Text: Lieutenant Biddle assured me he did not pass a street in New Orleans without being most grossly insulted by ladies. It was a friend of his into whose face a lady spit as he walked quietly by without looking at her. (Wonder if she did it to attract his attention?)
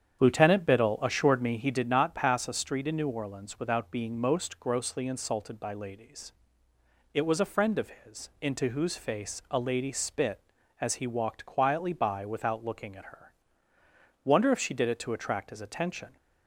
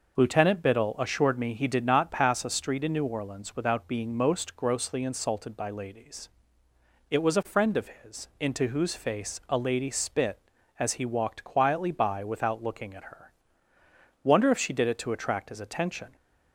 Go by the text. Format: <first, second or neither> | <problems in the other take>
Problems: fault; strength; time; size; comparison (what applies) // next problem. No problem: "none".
second | starts louder than the rest; strong; until 1.7 s; 8.5 dB